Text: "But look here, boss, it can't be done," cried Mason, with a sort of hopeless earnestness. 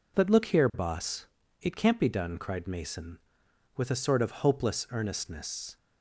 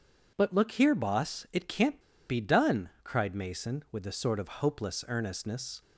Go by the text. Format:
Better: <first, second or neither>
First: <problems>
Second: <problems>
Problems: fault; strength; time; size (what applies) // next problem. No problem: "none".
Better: first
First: none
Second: pauses between "can't" and "be"; slight; at 2.0 s; 0.27 s long